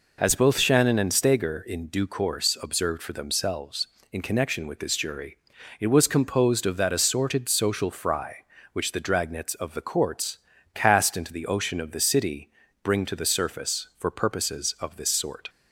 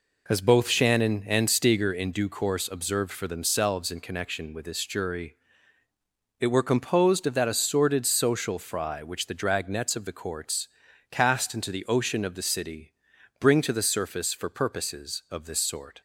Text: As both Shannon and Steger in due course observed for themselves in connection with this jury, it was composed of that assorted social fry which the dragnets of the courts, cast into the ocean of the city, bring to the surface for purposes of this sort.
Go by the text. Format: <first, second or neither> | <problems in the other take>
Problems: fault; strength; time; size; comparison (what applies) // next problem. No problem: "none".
first | says "were" for "was"; at 6.4 s